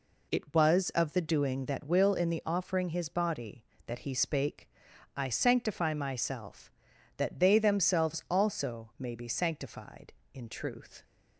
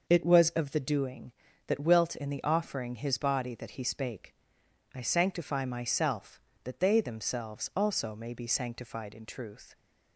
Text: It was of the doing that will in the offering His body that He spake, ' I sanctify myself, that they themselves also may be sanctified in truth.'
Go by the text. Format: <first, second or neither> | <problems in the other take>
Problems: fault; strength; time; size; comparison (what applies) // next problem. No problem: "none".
first | says "wilt" for "will"; at 1.8 s